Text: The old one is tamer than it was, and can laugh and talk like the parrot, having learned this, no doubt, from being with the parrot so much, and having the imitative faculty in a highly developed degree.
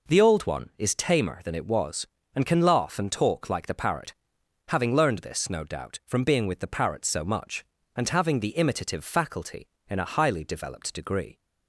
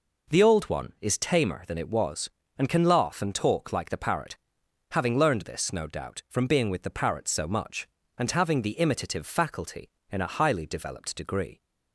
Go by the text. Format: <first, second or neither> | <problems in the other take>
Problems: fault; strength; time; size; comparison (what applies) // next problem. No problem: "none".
neither | none